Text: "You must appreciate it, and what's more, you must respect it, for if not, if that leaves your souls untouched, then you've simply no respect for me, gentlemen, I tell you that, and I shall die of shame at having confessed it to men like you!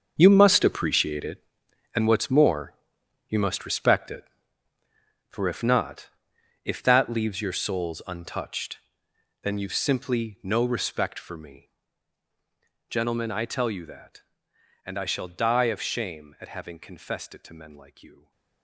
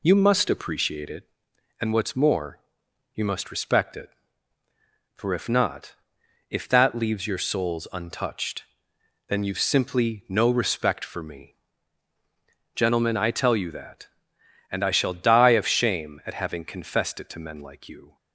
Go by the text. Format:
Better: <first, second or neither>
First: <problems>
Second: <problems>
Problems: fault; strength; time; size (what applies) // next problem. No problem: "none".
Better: second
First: gets quieter; strong; throughout; 14 dB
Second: none